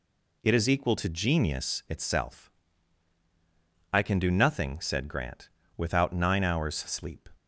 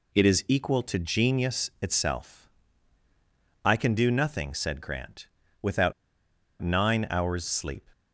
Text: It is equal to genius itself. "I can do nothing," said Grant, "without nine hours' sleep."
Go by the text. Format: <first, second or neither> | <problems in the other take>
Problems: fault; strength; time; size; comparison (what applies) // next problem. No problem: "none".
first | pauses between "without" and "nine"; noticeable; at 5.9 s; 0.69 s long